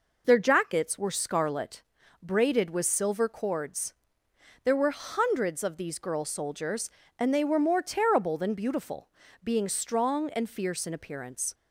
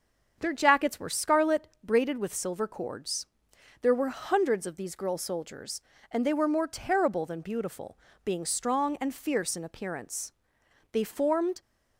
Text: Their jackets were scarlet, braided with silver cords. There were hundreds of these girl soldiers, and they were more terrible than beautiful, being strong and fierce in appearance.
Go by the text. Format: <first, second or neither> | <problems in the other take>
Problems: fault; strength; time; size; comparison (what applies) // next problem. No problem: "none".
first | starts louder than the rest; until 1.3 s; 7 dB // goes on to say "They formed"; noticeable; from 10.9 s on; 0.70 s long